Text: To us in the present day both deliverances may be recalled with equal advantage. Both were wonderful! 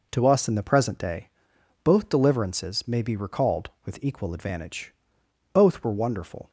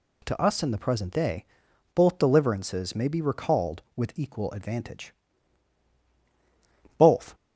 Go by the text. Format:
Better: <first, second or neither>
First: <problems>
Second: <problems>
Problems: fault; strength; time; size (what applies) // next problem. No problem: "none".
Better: first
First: pauses between "day" and "both"; noticeable; at 1.2 s; 0.56 s long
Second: pauses between "day" and "both"; noticeable; at 1.4 s; 0.50 s long // stops before "were wonderful"; at 7.3 s